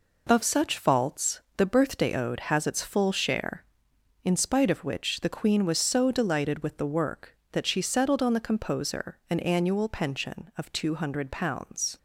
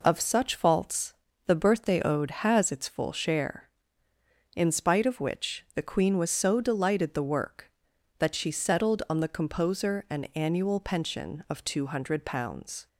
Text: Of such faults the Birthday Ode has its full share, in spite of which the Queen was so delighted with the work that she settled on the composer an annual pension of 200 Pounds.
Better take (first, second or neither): first